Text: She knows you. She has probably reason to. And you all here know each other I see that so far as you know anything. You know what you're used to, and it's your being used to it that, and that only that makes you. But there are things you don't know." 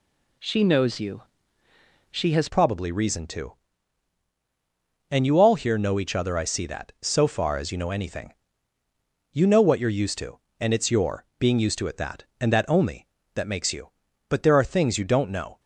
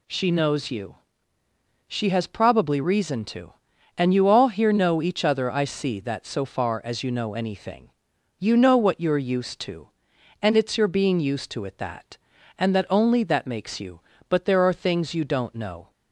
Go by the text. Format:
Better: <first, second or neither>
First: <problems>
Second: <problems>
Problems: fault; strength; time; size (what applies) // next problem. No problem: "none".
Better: second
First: changes voice at "probably"; from 2.4 s on; 13.1 s long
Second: none